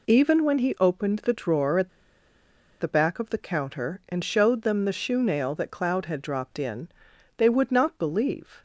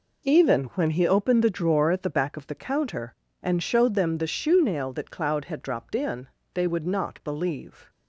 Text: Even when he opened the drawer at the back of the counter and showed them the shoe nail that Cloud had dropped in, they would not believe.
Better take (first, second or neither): second